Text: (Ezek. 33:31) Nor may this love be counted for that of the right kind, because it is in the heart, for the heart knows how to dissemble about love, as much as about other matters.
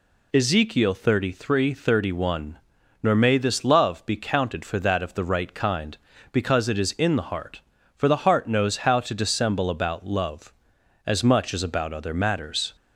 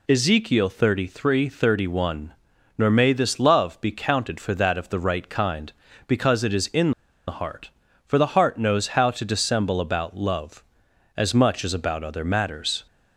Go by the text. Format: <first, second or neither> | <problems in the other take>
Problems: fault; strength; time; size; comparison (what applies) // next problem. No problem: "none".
first | pauses between "in" and "the"; slight; at 6.9 s; 0.35 s long